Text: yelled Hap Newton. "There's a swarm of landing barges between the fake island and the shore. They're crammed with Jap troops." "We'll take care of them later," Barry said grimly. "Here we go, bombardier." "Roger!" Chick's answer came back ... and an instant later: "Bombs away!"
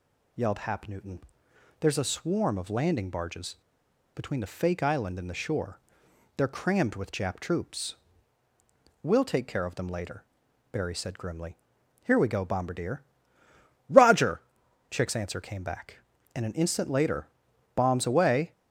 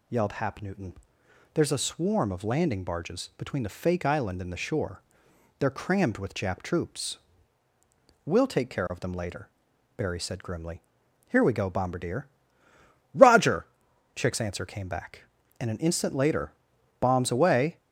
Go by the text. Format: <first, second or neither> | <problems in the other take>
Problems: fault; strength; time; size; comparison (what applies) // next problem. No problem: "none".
second | pauses between "barges" and "between"; noticeable; at 3.5 s; 0.57 s long